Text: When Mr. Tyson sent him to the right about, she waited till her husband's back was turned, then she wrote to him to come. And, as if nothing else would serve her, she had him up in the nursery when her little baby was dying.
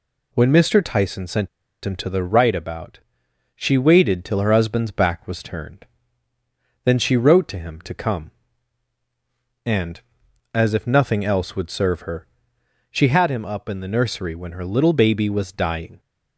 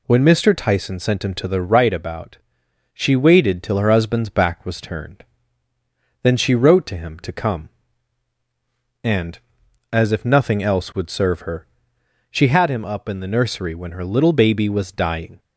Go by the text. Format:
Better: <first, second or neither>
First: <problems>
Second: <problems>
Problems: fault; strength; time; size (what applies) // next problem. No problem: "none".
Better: second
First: pauses between "sent" and "him"; at 1.4 s; 0.36 s long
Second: none